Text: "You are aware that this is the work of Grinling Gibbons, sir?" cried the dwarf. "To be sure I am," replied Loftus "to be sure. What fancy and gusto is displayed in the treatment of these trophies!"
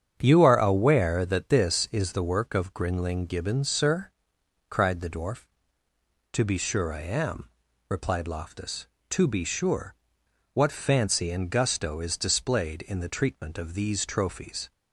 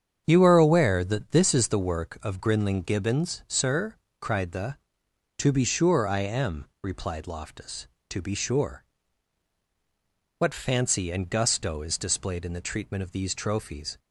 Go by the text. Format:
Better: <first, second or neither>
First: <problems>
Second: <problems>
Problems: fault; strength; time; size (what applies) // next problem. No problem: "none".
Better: first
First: starts louder than the rest; strong; until 1.2 s; 8.5 dB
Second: starts louder than the rest; strong; until 1.2 s; 7.5 dB // skips "dwarf"; at 5.0 s